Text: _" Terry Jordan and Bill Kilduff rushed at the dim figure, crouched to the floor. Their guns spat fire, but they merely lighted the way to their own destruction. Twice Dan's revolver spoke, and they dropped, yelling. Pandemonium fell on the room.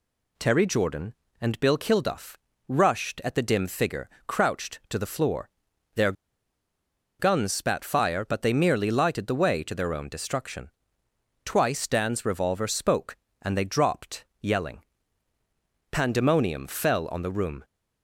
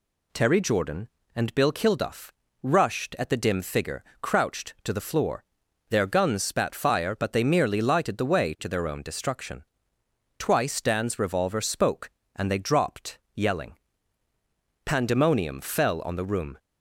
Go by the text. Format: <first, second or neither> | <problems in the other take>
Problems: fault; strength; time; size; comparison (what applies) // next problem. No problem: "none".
second | pauses between "Kilduff" and "rushed"; slight; at 2.3 s; 0.32 s long; slight in the second // pauses between "Their" and "guns"; at 6.1 s; 1.0 s long